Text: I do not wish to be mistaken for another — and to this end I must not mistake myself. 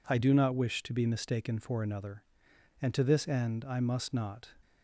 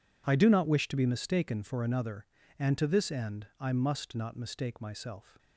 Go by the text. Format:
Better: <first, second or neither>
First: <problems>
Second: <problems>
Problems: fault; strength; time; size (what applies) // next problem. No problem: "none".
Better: second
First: stops before "mistake myself"; at 4.6 s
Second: none